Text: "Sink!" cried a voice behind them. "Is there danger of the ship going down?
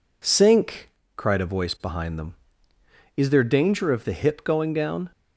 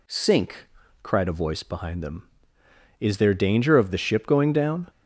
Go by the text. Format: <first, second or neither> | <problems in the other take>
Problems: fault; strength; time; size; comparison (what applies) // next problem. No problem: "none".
second | says "hip" for "ship"; at 4.1 s